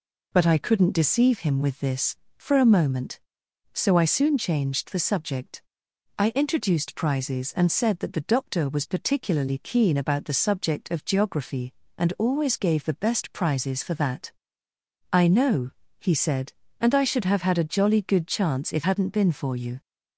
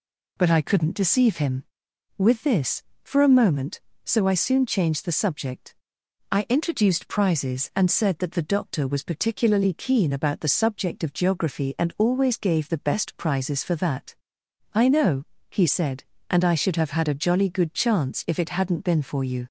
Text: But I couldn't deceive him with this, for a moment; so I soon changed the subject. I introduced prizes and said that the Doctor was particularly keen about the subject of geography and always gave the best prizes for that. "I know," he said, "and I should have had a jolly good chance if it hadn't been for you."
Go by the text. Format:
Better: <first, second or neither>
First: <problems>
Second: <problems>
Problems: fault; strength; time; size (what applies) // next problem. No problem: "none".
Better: second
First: skips "it"; at 18.8 s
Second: none